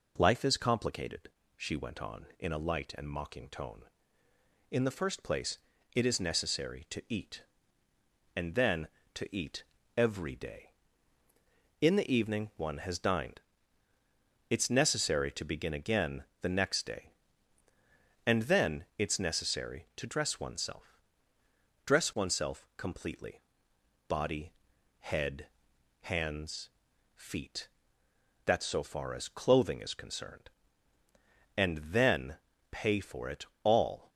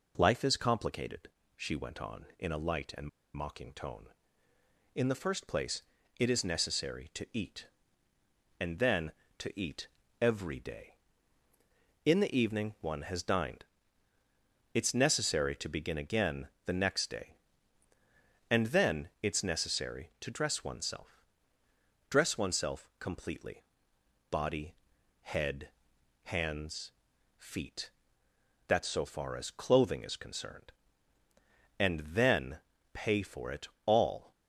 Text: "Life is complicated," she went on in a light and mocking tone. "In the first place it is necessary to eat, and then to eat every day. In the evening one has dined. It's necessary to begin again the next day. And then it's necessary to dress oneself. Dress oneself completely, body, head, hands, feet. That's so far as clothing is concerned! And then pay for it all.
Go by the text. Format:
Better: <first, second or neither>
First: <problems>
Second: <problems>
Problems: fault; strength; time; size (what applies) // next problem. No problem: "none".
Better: first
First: pauses between "place" and "it"; slight; at 5.5 s; 0.36 s long // pauses between "eat" and "every"; slight; at 9.6 s; 0.34 s long // pauses between "again" and "the"; slight; at 16.2 s; 0.16 s long // pauses between "then" and "pay"; slight; at 32.3 s; 0.32 s long // pauses between "it" and "all"; slight; at 33.4 s; 0.18 s long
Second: pauses between "and" and "mocking"; slight; at 3.0 s; 0.26 s long // pauses between "place" and "it"; slight; at 5.8 s; 0.36 s long // pauses between "eat" and "every"; slight; at 9.8 s; 0.34 s long // pauses between "again" and "the"; slight; at 16.4 s; 0.16 s long // pauses between "then" and "pay"; slight; at 32.6 s; 0.32 s long // pauses between "it" and "all"; slight; at 33.6 s; 0.18 s long